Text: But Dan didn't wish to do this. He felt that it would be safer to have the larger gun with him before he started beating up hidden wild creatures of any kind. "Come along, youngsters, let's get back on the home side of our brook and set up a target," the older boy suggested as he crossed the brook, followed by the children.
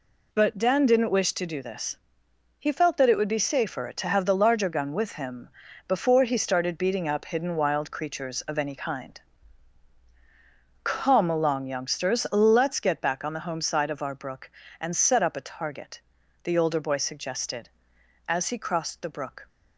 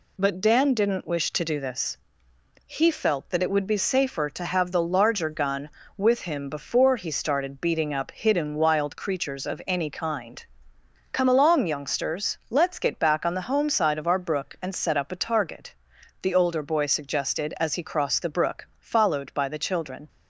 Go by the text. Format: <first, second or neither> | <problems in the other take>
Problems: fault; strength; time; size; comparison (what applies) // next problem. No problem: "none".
second | pauses between "him" and "before"; at 5.4 s; 0.38 s long // stops before "followed by the children"; at 19.4 s